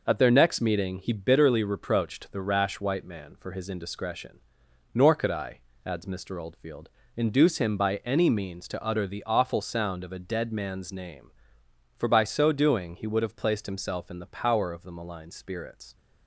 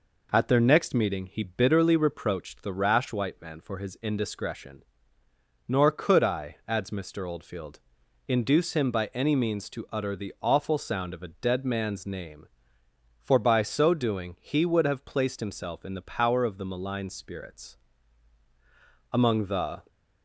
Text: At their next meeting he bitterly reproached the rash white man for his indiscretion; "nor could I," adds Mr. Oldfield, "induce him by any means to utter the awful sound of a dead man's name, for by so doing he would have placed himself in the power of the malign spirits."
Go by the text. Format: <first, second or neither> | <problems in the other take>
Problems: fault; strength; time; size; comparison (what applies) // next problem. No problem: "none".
first | goes on to say "Among the"; noticeable; from 19.1 s on; 0.70 s long